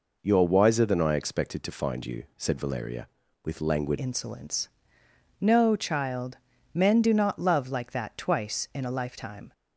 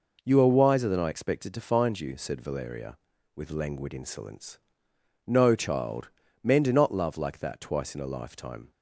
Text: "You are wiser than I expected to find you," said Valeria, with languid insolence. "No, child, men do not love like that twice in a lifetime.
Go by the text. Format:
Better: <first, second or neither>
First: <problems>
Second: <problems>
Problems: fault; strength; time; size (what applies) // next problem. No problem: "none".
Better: second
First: changes voice at "insolence"; from 3.9 s on; 5.6 s long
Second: none